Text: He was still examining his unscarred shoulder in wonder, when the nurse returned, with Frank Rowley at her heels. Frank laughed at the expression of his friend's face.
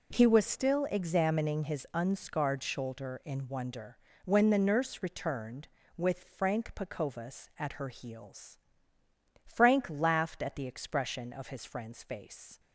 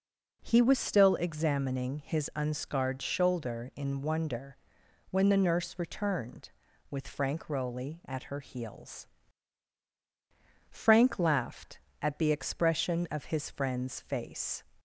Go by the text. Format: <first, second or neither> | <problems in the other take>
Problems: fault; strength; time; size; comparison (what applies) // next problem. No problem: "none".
second | says "Pacovas" for "Rowley"; at 6.7 s